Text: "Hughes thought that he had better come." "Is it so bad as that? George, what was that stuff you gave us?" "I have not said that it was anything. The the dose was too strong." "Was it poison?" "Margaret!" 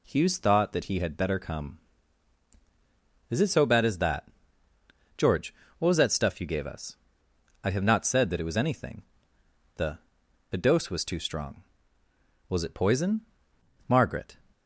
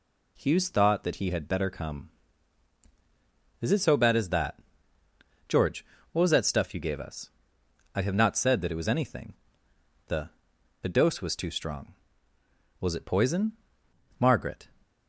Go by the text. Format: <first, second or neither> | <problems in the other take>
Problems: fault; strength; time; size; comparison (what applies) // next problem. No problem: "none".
neither | pauses between "The" and "the"; noticeable; the same in both